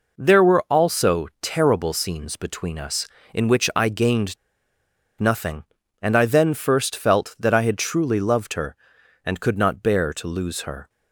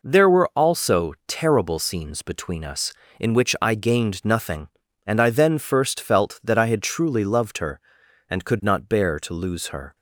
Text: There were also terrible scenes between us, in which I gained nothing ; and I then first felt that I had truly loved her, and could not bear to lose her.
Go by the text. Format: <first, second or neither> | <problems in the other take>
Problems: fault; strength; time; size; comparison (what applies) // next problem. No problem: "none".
second | pauses between "gained" and "nothing"; noticeable; at 4.3 s; 0.84 s long